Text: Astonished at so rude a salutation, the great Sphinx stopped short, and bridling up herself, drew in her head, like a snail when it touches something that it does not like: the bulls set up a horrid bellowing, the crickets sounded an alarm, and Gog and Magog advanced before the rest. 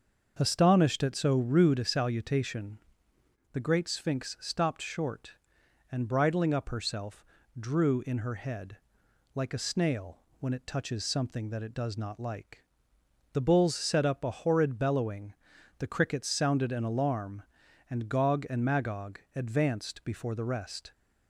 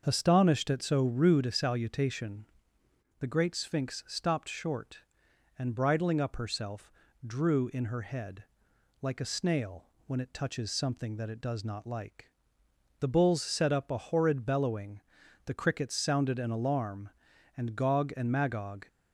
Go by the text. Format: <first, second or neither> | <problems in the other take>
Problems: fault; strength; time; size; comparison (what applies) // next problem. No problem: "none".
first | starts louder than the rest; until 1.0 s; 6.5 dB; also in the first // pauses between "snail" and "when"; slight; at 9.8 s; 0.20 s long; slight in the first // stops before "advanced before the rest"; at 18.8 s